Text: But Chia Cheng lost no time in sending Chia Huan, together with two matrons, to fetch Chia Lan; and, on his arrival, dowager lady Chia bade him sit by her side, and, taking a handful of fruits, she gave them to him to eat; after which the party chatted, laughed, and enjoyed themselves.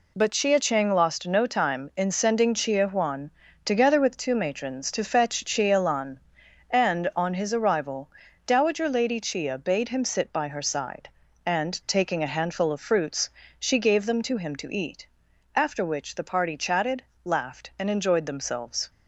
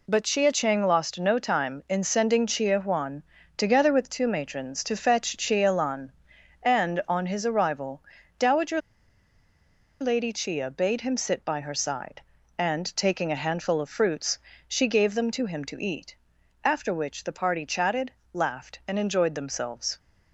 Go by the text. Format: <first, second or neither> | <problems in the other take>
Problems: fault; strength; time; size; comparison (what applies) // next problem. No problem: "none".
first | pauses between "dowager" and "lady"; at 8.8 s; 1.2 s long